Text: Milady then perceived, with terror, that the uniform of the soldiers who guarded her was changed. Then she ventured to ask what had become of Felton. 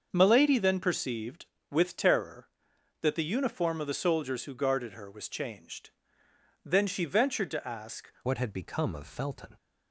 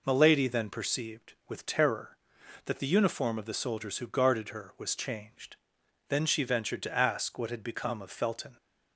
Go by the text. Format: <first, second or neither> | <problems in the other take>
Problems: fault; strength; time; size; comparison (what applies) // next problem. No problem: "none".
second | starts louder than the rest; until 1.1 s; 6.5 dB // changes voice at "what"; from 8.2 s on; 1.3 s long